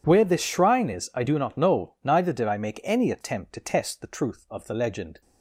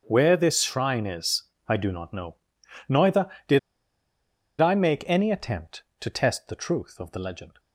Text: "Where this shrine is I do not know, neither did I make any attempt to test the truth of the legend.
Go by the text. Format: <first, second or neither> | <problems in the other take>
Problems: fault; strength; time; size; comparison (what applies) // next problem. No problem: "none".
first | starts louder than the rest; until 1.0 s; 7 dB // pauses between "is" and "I"; slight; at 1.4 s; 0.22 s long // pauses between "did" and "I"; at 3.5 s; 1.0 s long